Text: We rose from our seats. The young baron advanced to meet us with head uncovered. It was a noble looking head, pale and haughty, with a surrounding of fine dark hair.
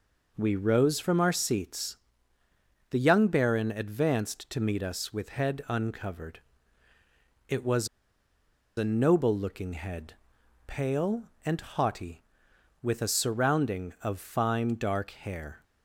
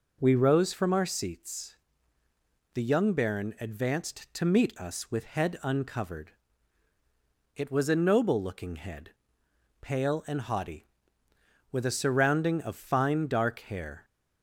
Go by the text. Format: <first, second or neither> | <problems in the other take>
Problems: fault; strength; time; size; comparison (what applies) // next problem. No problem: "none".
second | pauses between "was" and "a"; noticeable; at 7.8 s; 0.89 s long